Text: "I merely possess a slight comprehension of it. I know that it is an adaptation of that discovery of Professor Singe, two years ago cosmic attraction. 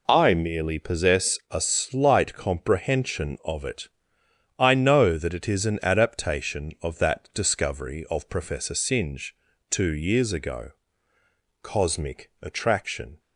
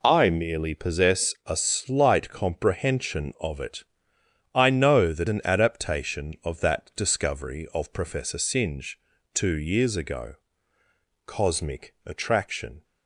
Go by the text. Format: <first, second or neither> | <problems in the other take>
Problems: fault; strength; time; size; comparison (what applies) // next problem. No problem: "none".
first | skips "it is"; at 5.2 s // pauses between "ago" and "cosmic"; noticeable; at 10.3 s; 0.90 s long; noticeable in the first